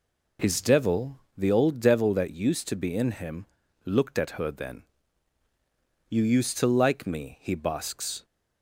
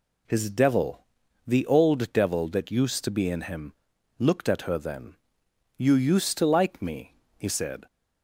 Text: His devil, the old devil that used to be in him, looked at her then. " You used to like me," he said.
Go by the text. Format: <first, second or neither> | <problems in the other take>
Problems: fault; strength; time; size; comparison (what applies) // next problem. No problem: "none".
second | says "basks" for "said"; at 7.5 s